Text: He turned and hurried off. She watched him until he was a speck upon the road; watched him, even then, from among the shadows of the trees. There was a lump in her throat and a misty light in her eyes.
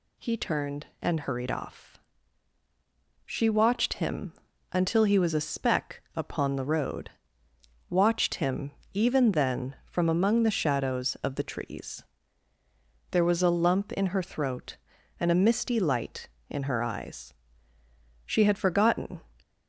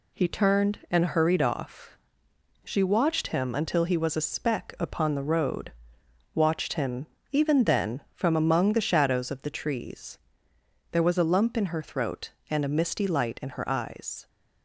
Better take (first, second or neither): second